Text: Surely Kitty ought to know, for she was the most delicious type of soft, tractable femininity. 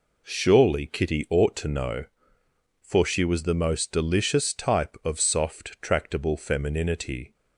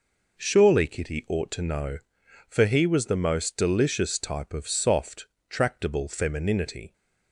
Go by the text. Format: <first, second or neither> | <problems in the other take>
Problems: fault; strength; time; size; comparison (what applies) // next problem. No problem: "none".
first | says "he" for "she"; at 2.6 s